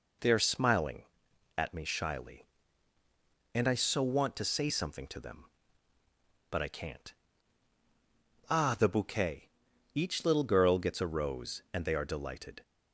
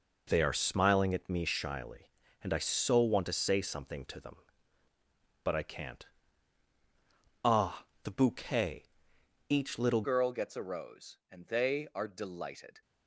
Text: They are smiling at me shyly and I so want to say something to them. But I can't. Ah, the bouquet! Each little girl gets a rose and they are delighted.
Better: first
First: none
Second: changes voice at "girl"; from 10.0 s on; 2.8 s long

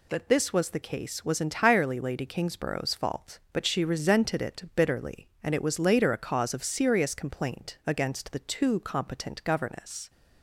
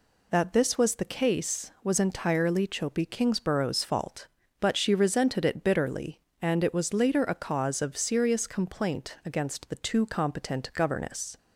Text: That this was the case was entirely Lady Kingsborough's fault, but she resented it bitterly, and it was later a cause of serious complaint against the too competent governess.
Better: first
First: none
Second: says "Chopi" for "Lady"; at 2.6 s

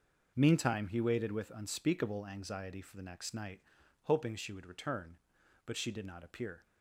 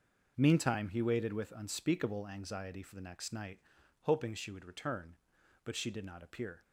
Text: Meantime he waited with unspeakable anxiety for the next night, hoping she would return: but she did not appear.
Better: neither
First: none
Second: none

